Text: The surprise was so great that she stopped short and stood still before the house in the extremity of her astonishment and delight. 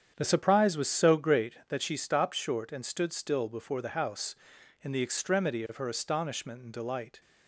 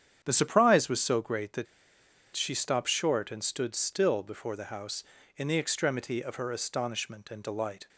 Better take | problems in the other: first | starts louder than the rest; strong; until 1.2 s; 8.5 dB; strong in the first // pauses between "that" and "she"; noticeable; at 1.6 s; 0.68 s long

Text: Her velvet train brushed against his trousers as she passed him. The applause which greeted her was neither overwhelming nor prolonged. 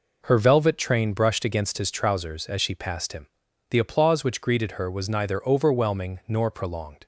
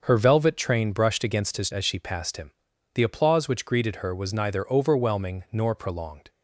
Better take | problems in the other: first | starts louder than the rest; until 1.0 s; 6.5 dB // skips "trousers"; at 1.7 s

